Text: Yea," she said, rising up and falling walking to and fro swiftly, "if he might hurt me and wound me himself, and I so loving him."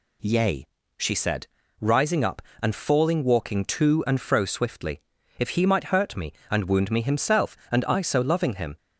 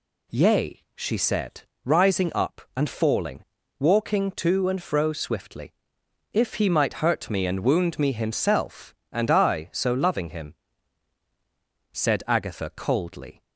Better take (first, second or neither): first